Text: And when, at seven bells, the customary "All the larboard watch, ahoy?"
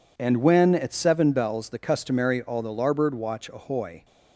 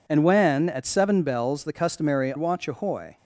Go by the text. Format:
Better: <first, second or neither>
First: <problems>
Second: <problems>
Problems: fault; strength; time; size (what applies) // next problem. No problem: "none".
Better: first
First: none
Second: skips "All the larboard"; at 2.3 s